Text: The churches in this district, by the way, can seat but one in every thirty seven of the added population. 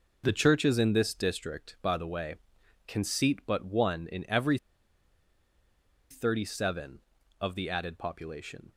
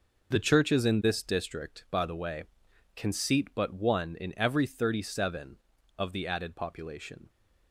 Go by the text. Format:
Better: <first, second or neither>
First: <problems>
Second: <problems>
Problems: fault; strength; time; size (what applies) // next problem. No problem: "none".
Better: second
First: pauses between "every" and "thirty"; strong; at 4.5 s; 1.5 s long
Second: none